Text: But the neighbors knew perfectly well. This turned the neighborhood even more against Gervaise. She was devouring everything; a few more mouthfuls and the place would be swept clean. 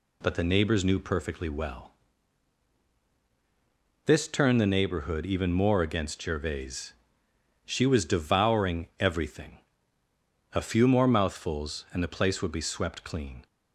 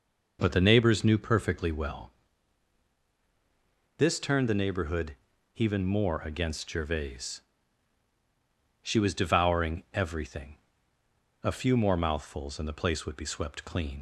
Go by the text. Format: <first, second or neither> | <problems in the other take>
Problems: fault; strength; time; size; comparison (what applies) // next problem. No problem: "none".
first | pauses between "neighborhood" and "even"; at 5.1 s; 0.40 s long // leaves "clean" unfinished; at 13.9 s; 75 ms